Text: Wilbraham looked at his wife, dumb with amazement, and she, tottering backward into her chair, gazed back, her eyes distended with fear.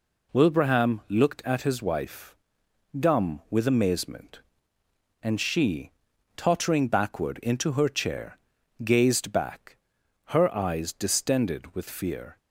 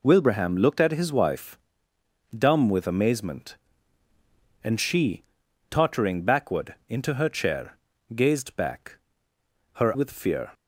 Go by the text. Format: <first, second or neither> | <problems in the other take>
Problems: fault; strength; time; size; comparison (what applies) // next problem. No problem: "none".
first | skips "eyes distended"; at 9.9 s